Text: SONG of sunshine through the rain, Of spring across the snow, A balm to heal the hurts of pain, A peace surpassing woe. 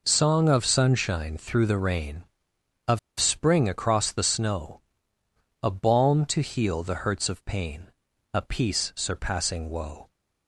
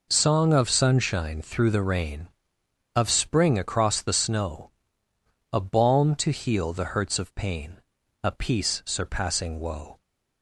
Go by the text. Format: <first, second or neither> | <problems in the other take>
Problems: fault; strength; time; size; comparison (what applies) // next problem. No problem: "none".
second | pauses between "Of" and "spring"; slight; at 2.9 s; 0.20 s long